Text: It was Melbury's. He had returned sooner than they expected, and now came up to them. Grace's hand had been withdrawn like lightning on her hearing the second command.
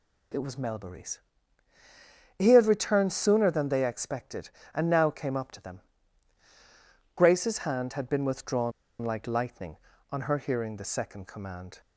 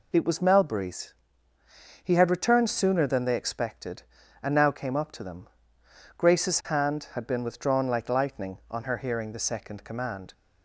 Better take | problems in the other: second | pauses between "withdrawn" and "like"; slight; at 8.7 s; 0.30 s long

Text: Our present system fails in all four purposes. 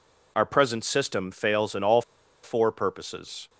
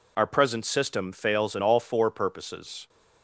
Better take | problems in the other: second | pauses between "all" and "four"; at 2.0 s; 0.41 s long

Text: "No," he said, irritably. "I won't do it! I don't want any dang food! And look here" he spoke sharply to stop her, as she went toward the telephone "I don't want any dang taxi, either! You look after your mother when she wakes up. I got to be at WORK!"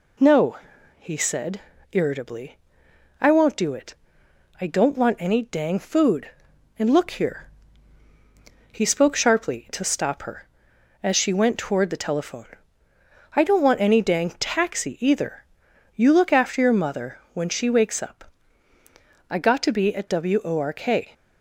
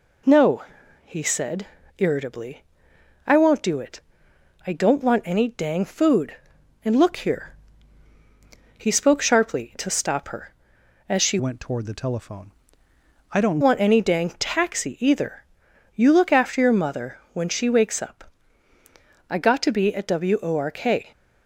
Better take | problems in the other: first | pauses between "here" and "he"; at 7.5 s; 1.2 s long; also in the first // changes voice from "went" to "don't"; from 11.3 to 13.6 s; 2.3 s long // pauses between "telephone" and "I"; noticeable; at 12.4 s; 0.82 s long; noticeable in the first // pauses between "mother" and "when"; slight; at 17.1 s; 0.16 s long; slight in the first

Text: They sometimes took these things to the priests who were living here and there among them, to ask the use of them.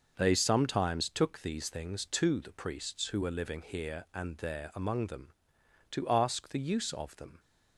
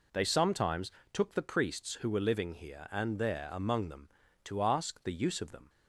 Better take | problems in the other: first | pauses between "sometimes" and "took"; slight; at 0.8 s; 0.22 s long // skips "these things to"; at 1.3 s

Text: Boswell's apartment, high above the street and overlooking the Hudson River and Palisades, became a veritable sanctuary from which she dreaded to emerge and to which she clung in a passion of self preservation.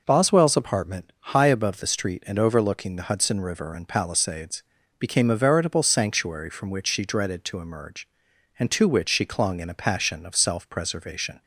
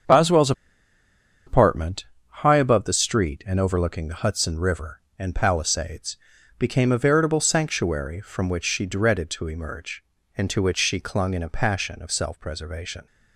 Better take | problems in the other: first | starts louder than the rest; until 2.0 s; 7 dB // pauses between "Boswell's" and "apartment"; noticeable; at 0.5 s; 0.94 s long

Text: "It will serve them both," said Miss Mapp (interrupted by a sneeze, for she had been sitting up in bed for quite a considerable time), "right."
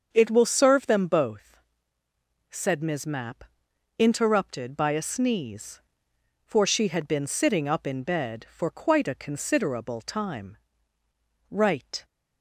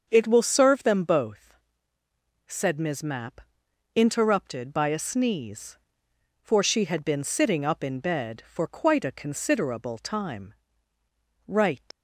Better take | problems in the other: first | starts louder than the rest; until 1.1 s; 6.5 dB; also in the first // leaves "right" unfinished; at 11.9 s; 105 ms

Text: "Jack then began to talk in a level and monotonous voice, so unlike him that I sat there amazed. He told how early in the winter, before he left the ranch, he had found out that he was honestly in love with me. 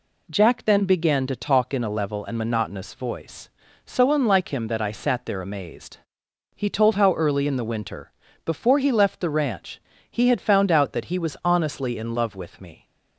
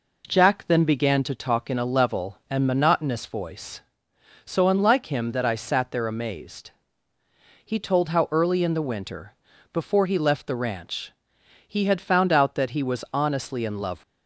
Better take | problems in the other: first | stops before "with me"; at 14.0 s

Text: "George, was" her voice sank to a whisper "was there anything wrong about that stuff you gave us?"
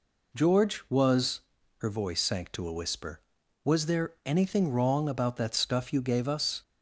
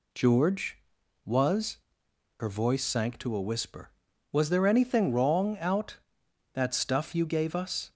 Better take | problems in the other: first | pauses between "was" and "her"; noticeable; at 1.7 s; 0.64 s long; also in the first // says "out" for "about"; at 5.5 s

